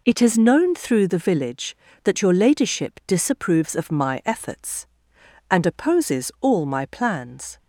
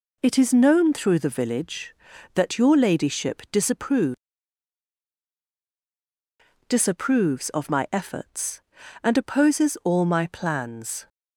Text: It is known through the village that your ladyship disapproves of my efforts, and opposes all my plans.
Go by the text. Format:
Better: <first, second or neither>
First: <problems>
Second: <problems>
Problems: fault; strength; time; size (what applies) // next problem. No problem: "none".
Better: first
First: none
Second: says "disapproves" twice; at 6.6 s